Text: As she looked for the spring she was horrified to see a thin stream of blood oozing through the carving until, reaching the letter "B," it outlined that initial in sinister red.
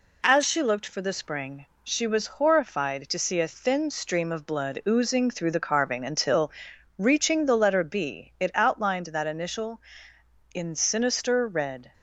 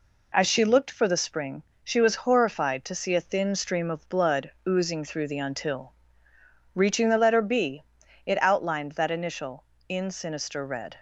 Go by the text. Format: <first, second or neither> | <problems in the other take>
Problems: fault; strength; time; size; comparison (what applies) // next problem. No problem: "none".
first | pauses between "spring" and "she"; slight; at 1.6 s; 0.22 s long; slight in the first // pauses between "blood" and "oozing"; slight; at 4.4 s; 0.16 s long // skips "carving"; at 5.3 s